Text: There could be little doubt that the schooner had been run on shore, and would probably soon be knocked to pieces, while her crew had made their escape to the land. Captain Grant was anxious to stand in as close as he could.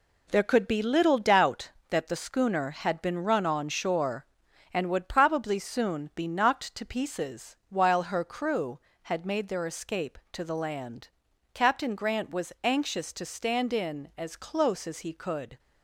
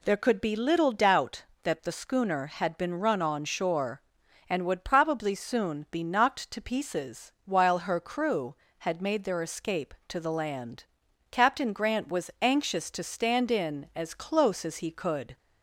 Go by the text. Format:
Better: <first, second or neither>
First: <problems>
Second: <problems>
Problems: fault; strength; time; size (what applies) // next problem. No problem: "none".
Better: second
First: gets quieter; strong; throughout; 7.5 dB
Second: none